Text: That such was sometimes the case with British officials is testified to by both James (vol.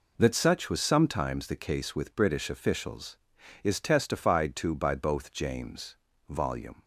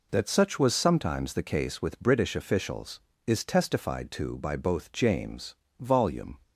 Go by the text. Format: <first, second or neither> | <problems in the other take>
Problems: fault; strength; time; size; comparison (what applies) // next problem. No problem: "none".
neither | none